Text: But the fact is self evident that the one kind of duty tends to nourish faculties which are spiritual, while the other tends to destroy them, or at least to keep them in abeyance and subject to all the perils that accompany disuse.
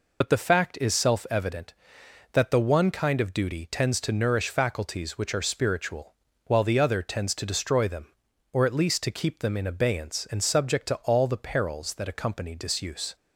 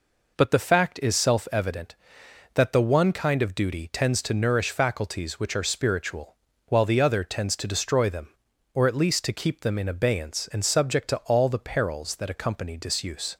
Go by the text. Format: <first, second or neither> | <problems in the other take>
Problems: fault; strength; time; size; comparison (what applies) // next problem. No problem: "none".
second | loses the start of "But"; at 0.2 s; 55 ms